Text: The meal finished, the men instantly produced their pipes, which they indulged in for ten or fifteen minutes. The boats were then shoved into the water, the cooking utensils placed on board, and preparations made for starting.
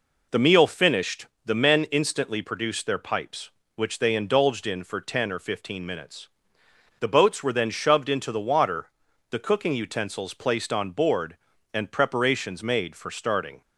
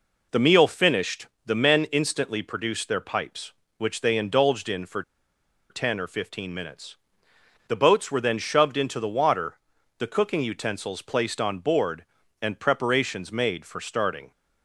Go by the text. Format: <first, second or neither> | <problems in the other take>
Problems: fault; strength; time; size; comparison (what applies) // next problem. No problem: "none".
first | pauses between "for" and "ten"; noticeable; at 5.0 s; 0.68 s long